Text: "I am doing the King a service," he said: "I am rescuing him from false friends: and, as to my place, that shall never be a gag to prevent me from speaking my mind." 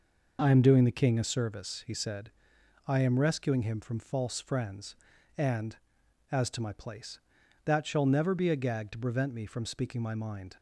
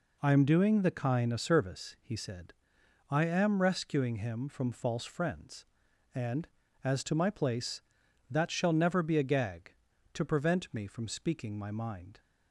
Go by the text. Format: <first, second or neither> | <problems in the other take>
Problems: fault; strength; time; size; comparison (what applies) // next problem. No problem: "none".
first | says "Kine" for "King"; at 0.9 s